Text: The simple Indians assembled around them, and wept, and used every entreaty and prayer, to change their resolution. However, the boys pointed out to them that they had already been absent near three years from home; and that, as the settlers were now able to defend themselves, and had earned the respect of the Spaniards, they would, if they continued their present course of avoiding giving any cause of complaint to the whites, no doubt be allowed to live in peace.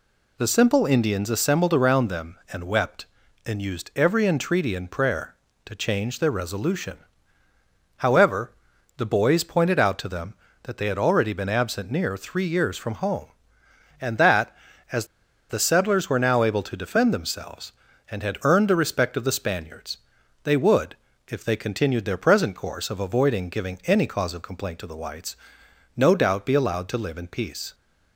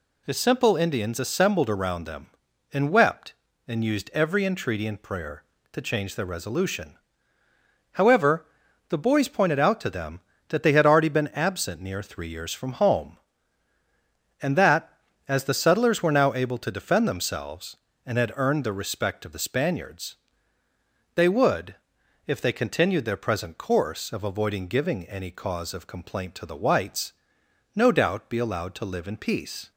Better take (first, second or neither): second